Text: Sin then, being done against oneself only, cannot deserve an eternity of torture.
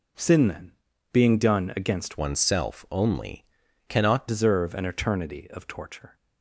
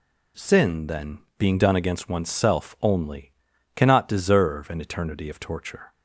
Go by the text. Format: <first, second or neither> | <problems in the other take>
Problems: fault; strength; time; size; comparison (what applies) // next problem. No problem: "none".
second | changes voice from "oneself" to "cannot"; from 2.1 to 4.2 s; 2.1 s long